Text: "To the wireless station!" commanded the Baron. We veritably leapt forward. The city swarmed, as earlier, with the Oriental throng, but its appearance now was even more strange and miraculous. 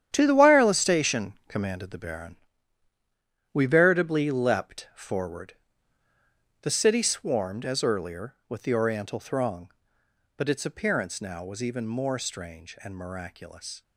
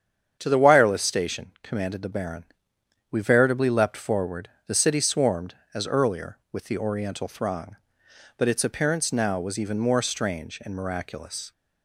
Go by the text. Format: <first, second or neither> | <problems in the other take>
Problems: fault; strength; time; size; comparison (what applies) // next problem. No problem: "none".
second | gets quieter; strong; throughout; 11 dB // starts louder than the rest; strong; until 1.1 s; 10 dB; strong in the second